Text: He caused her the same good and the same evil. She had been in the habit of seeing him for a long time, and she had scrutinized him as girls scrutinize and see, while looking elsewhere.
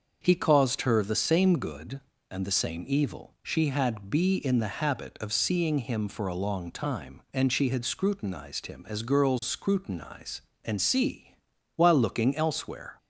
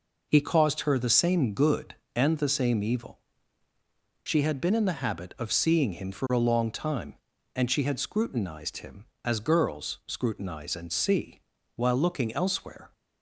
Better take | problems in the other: second | starts louder than the rest; until 1.2 s; 6.5 dB // says "be" for "been"; at 4.0 s

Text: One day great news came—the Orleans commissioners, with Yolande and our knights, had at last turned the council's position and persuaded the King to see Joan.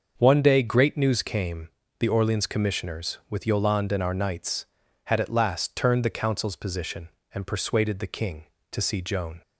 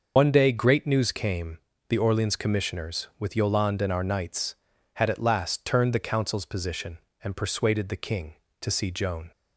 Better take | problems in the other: first | loses the start of "One"; at 0.1 s; 90 ms // starts louder than the rest; until 1.1 s; 6 dB; also in the first

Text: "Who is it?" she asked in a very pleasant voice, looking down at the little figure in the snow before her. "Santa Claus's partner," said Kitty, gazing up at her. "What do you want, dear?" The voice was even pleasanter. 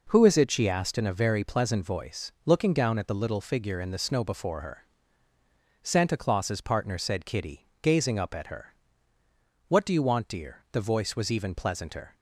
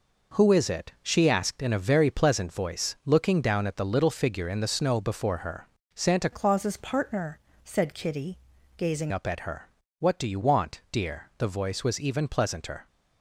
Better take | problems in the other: first | changes voice from "Claus's" to "gazing"; from 6.3 to 9.1 s; 2.8 s long

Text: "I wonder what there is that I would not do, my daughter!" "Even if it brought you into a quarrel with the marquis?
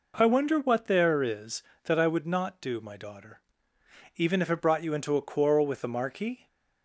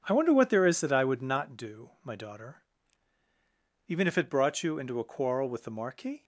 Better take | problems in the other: neither | none

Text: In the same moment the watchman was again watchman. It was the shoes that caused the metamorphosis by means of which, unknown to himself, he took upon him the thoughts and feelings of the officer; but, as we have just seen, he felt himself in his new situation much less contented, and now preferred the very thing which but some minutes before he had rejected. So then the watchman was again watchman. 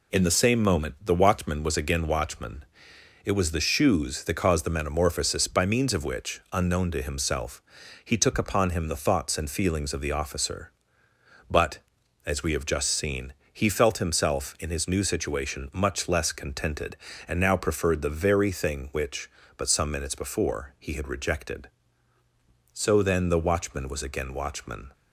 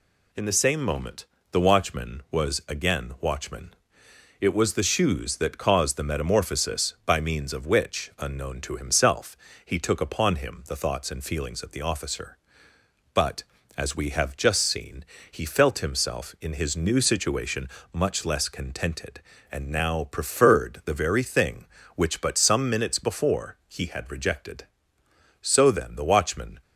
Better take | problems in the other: first | pauses between "moment" and "the"; slight; at 1.2 s; 0.26 s long // pauses between "situation" and "much"; slight; at 17.6 s; 0.24 s long // stops before "was again watchman"; at 26.6 s

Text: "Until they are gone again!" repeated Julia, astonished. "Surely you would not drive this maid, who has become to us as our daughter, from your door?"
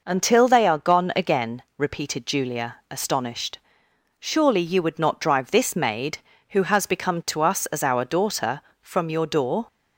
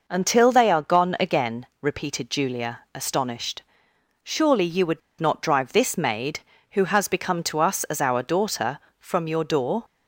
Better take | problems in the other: first | pauses between "would" and "not"; slight; at 5.0 s; 0.20 s long

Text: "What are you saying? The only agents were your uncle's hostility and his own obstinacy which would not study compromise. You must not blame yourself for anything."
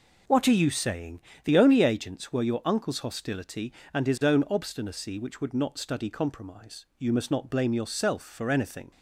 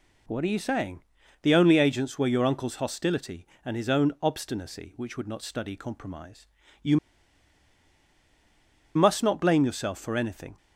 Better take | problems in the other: first | pauses between "You" and "must"; strong; at 6.9 s; 1.9 s long

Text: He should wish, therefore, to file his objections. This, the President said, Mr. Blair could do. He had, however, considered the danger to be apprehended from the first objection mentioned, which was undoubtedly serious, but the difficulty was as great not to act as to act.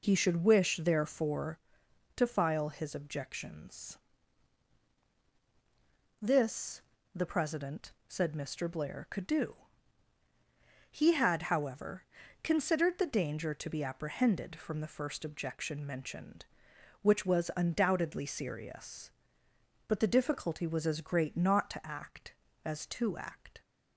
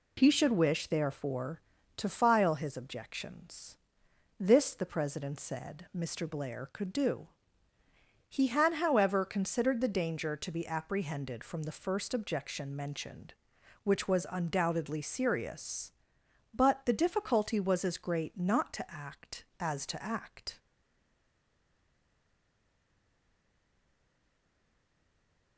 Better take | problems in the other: first | stays silent after the last word; strong; from 20.5 s on; 5.0 s long

